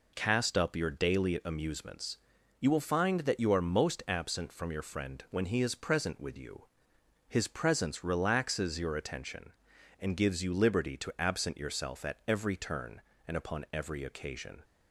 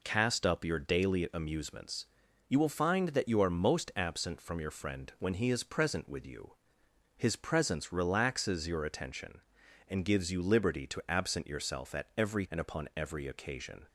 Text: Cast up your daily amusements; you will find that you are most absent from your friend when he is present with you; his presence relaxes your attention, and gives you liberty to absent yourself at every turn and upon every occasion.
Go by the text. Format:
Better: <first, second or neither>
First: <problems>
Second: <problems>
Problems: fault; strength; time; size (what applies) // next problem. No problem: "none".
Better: first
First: none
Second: skips "turn"; at 12.4 s